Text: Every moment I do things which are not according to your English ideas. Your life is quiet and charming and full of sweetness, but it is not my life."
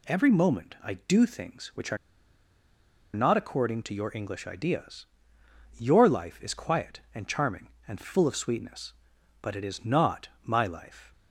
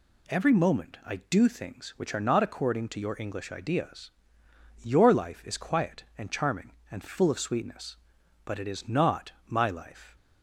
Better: second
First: pauses between "are" and "not"; at 1.9 s; 1.1 s long // pauses between "not" and "my"; slight; at 10.2 s; 0.16 s long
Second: pauses between "not" and "my"; slight; at 9.3 s; 0.16 s long

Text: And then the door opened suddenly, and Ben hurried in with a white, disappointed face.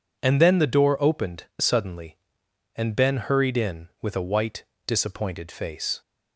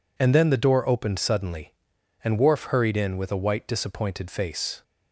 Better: first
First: none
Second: says "Worf" for "Ben"; at 2.3 s

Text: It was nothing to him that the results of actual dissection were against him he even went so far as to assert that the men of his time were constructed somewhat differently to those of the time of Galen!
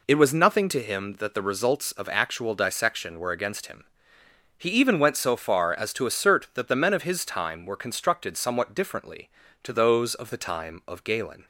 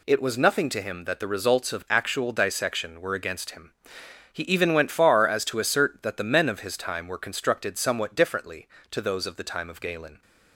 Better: first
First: pauses between "him" and "he"; noticeable; at 3.8 s; 0.70 s long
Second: pauses between "him" and "he"; noticeable; at 3.7 s; 0.60 s long // skips "so"; at 4.8 s

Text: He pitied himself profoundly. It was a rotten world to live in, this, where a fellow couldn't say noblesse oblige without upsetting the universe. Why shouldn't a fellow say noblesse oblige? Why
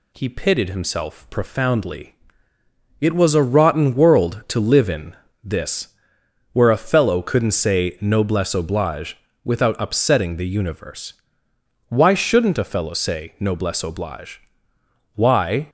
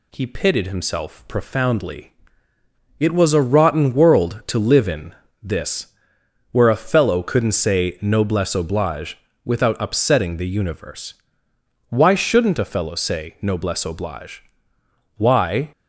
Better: neither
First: pauses between "oblige" and "without"; slight; at 9.1 s; 0.28 s long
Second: pauses between "oblige" and "without"; slight; at 9.1 s; 0.28 s long

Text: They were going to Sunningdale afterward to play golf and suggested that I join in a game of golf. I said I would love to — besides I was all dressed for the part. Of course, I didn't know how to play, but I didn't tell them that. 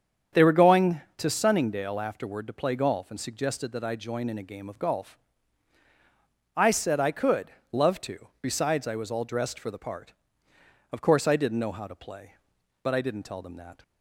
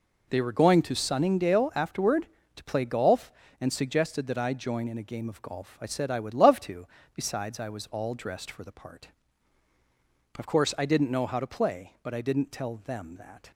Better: second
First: starts louder than the rest; strong; until 1.5 s; 8 dB // says "could" for "would"; at 7.1 s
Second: none

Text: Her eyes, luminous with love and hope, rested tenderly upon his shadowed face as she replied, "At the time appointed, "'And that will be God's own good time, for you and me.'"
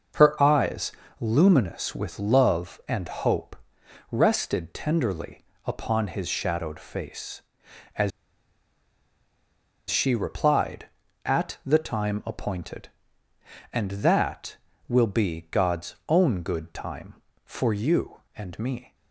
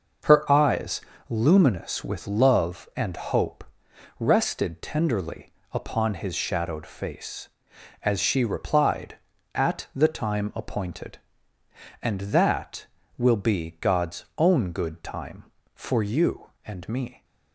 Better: second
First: pauses between "tenderly" and "upon"; slight; at 5.4 s; 0.22 s long // pauses between "as" and "she"; strong; at 8.1 s; 1.7 s long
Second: pauses between "tenderly" and "upon"; slight; at 5.5 s; 0.20 s long

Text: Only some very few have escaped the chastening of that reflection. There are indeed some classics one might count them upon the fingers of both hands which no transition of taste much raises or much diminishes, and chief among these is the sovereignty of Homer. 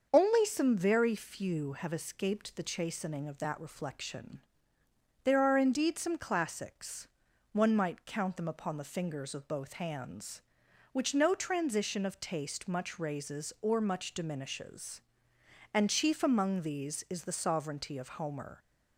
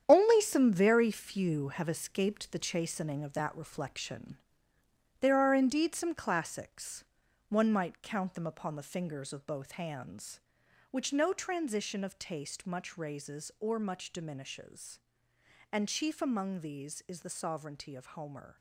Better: first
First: starts louder than the rest; until 1.1 s; 6.5 dB // pauses between "classics" and "one"; at 7.0 s; 0.42 s long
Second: gets quieter; strong; throughout; 9 dB // starts louder than the rest; strong; until 1.0 s; 9 dB // pauses between "classics" and "one"; at 7.0 s; 0.42 s long

